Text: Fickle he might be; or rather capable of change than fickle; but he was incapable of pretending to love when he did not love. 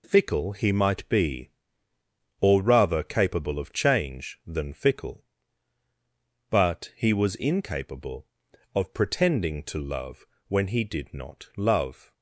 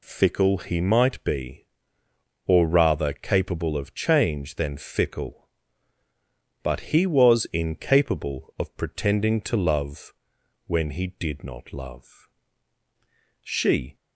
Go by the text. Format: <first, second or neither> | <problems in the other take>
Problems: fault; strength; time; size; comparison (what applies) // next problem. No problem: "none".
first | pauses between "love" and "when"; noticeable; at 10.1 s; 0.54 s long; slight in the first // goes on to say "She"; from 13.4 s on; 0.54 s long